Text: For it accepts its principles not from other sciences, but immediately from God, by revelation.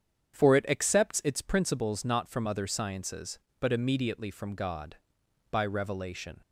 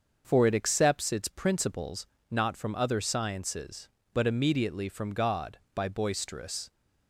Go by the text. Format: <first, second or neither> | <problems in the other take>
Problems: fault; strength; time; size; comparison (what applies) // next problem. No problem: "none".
first | starts louder than the rest; until 1.2 s; 6.5 dB; strong in the first // pauses between "principles" and "not"; slight; at 2.0 s; 0.24 s long // says "boisterous" for "revelation"; at 5.8 s